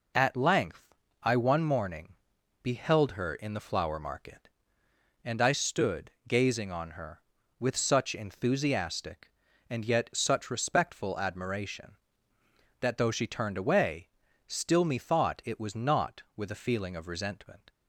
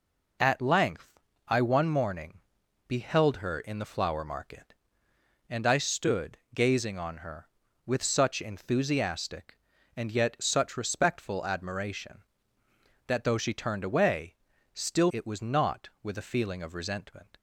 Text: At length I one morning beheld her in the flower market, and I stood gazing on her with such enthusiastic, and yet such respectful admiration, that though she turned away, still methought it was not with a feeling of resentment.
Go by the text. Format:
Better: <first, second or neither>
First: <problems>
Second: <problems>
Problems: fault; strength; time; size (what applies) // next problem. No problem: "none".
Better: first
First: pauses between "length" and "I"; slight; at 0.9 s; 0.26 s long // pauses between "morning" and "beheld"; noticeable; at 2.1 s; 0.48 s long // pauses between "stood" and "gazing"; slight; at 6.1 s; 0.16 s long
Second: pauses between "length" and "I"; slight; at 1.1 s; 0.26 s long // pauses between "morning" and "beheld"; noticeable; at 2.3 s; 0.48 s long // pauses between "stood" and "gazing"; slight; at 6.3 s; 0.16 s long // skips "methought"; at 15.1 s